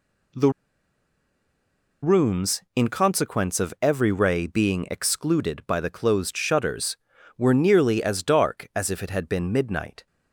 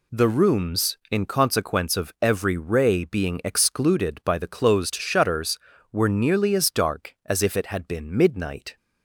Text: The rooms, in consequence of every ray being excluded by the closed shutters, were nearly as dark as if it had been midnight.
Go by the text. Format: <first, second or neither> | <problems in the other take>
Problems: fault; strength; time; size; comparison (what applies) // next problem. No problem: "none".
second | pauses between "The" and "rooms"; strong; at 0.4 s; 1.5 s long